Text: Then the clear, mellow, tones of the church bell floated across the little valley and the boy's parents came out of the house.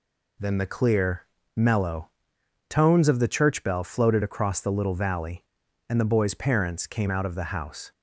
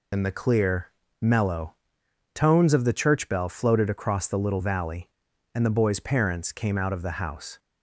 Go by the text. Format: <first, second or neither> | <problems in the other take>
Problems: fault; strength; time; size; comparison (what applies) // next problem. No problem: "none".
first | loses the start of "Then"; at 0.1 s; 75 ms